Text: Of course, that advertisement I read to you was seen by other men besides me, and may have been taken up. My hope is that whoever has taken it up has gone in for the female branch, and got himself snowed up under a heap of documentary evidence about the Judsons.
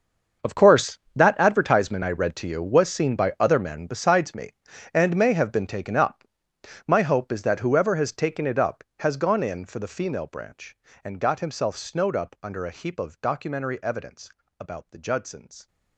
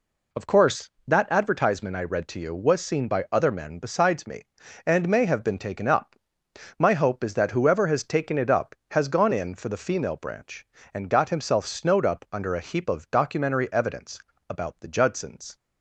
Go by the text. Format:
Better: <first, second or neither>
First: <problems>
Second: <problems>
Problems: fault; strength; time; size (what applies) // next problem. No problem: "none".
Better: second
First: gets quieter; strong; throughout; 16 dB // pauses between "evidence" and "about"; slight; at 14.3 s; 0.30 s long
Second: pauses between "evidence" and "about"; slight; at 14.2 s; 0.30 s long